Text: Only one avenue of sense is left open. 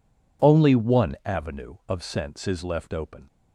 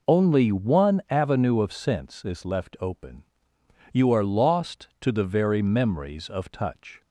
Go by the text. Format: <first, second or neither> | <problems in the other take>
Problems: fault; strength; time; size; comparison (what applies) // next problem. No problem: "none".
first | goes on to say "You are lost to the very memories of touch"; strong; from 3.9 s on; 3.0 s long